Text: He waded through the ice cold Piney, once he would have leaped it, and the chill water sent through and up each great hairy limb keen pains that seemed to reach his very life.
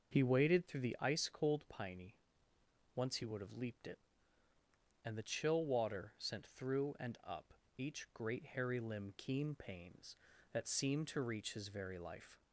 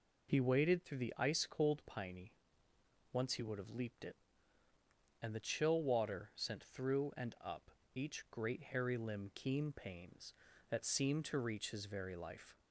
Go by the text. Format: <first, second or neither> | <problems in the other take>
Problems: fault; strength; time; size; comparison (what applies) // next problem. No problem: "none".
second | starts louder than the rest; noticeable; until 1.1 s; 6 dB // pauses between "up" and "each"; slight; at 7.5 s; 0.24 s long; slight in the second